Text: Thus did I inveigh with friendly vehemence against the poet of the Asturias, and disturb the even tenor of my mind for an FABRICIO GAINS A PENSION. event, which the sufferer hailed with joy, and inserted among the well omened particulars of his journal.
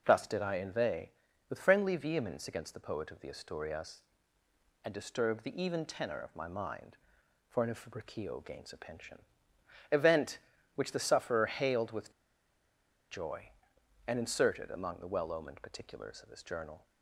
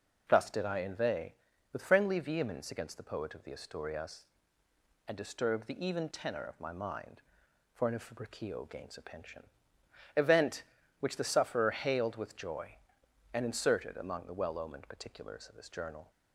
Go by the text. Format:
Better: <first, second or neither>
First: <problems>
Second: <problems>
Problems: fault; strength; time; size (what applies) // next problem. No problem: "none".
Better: second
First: pauses between "with" and "joy"; at 12.1 s; 0.99 s long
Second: none